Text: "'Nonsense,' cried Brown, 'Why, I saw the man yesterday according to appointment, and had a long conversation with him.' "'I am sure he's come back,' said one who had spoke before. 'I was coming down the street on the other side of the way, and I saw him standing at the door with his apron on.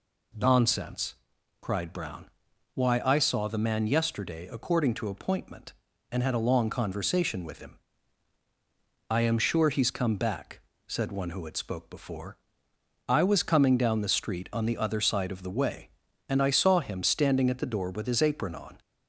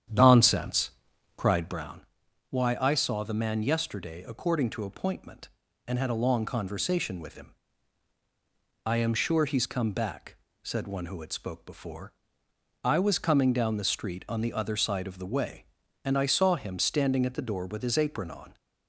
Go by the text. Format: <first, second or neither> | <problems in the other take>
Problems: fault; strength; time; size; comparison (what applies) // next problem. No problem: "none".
first | starts louder than the rest; strong; until 1.9 s; 9.5 dB